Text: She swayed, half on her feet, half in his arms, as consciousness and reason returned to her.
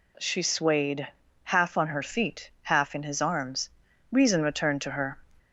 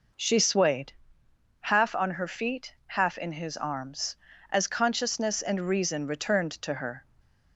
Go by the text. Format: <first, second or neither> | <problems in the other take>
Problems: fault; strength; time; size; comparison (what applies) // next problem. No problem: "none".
second | skips "as consciousness and"; at 3.8 s